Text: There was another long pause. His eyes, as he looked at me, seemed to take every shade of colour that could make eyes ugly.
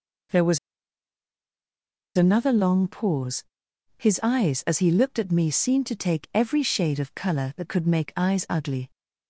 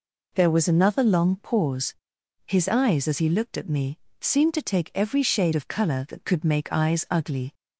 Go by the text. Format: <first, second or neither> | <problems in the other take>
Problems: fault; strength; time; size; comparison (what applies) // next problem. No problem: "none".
second | pauses between "was" and "another"; strong; at 0.5 s; 1.5 s long